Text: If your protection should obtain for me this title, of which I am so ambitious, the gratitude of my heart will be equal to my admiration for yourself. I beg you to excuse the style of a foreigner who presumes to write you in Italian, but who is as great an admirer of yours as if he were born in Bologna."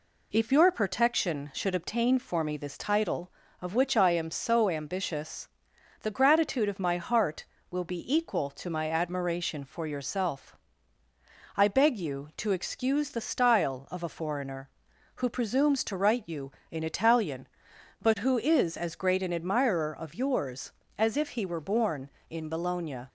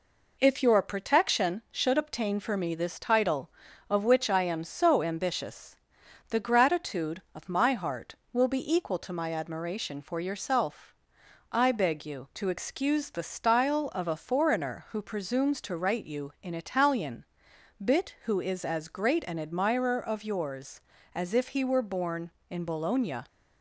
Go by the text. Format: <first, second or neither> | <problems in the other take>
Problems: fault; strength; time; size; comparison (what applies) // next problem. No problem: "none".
first | says "bit" for "but"; at 17.8 s